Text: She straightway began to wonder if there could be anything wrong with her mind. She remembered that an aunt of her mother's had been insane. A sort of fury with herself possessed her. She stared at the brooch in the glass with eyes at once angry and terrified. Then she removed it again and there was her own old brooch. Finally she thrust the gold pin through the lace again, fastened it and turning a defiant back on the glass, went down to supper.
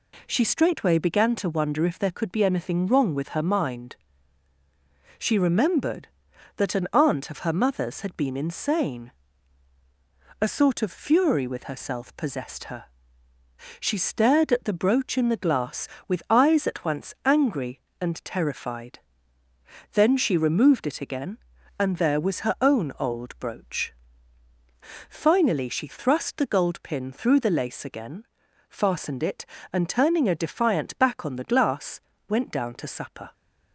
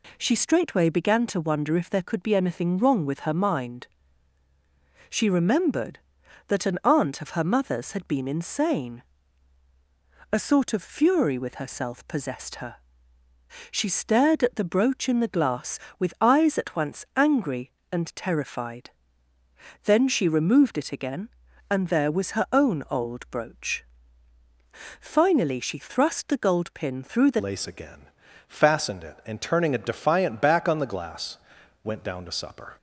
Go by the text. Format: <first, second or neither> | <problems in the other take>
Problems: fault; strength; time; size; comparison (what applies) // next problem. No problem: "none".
first | changes voice at "lace"; from 27.3 s on; 5.4 s long